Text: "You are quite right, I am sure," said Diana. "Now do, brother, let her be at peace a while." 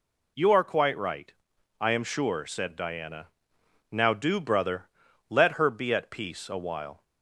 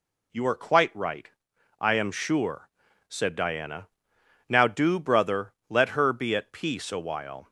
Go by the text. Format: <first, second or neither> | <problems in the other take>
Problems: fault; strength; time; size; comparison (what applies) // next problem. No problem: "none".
neither | none